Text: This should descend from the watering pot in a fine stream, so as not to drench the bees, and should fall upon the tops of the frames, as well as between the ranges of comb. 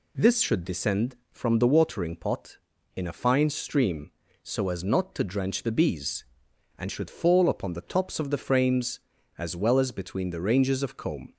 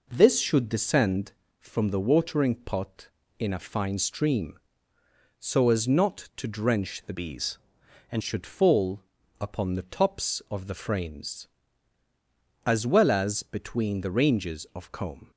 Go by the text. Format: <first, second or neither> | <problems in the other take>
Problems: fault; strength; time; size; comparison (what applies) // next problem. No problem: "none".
first | changes voice from "bees" to "and"; from 7.1 to 8.2 s; 1.1 s long // pauses between "fall" and "upon"; at 9.0 s; 0.38 s long